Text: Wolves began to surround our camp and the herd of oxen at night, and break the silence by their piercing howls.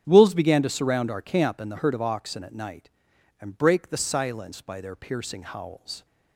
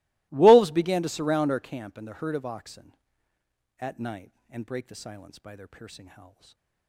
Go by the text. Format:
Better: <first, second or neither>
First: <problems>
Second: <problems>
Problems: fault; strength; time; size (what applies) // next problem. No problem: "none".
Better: first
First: starts louder than the rest; strong; until 1.0 s; 8.5 dB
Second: gets quieter; strong; throughout; 25.5 dB // starts louder than the rest; strong; until 1.3 s; 23.5 dB // stays silent after the last word; slight; from 6.2 s on; 0.6 s long